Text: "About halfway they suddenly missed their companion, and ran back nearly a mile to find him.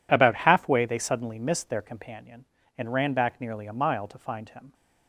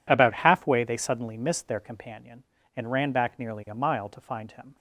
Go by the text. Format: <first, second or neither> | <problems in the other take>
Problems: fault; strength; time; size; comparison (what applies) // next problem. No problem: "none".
neither | none